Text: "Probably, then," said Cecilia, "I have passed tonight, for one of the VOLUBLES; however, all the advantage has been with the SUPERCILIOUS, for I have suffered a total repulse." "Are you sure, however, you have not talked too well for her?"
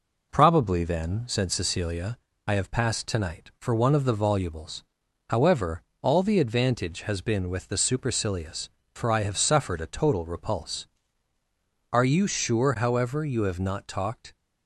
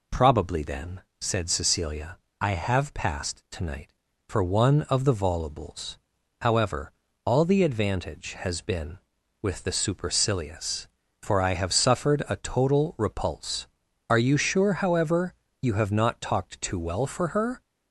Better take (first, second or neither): second